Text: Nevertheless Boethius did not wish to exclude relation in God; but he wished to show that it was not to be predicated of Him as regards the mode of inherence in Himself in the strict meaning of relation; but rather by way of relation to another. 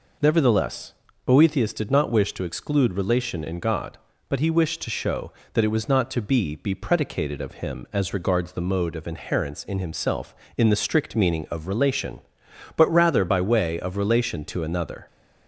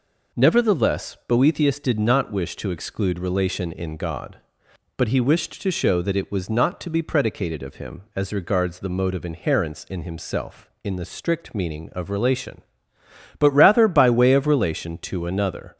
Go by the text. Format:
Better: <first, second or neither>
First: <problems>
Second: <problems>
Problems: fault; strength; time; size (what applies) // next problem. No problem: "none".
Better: second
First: pauses between "Nevertheless" and "Boethius"; slight; at 0.9 s; 0.32 s long // says "be" twice; at 6.5 s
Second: none